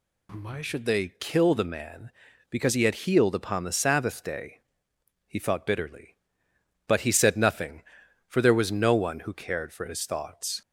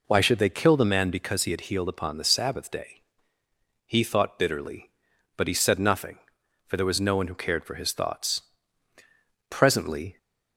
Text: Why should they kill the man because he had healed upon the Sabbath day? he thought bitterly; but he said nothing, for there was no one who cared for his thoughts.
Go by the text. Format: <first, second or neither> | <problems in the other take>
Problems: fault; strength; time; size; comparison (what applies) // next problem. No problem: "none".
first | goes on to say "Presently"; noticeable; from 9.4 s on; 0.68 s long